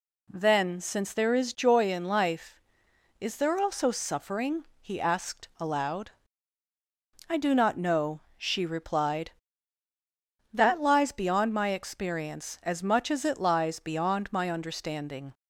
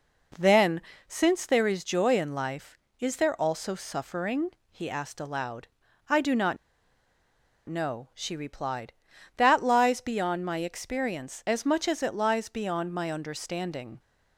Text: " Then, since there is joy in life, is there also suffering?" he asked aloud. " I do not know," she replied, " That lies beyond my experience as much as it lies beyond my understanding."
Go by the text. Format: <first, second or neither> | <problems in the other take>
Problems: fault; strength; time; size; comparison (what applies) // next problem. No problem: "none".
first | pauses between "not" and "know"; at 6.5 s; 1.1 s long